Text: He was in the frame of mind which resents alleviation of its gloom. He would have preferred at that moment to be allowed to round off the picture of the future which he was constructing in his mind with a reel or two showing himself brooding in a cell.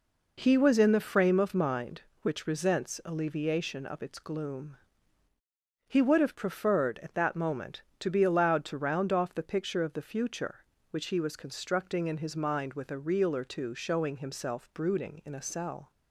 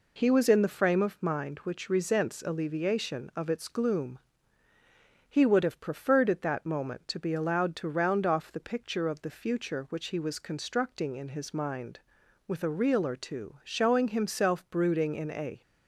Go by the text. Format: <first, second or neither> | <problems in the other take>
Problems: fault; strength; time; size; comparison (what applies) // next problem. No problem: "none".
first | stops before "cell"; at 15.6 s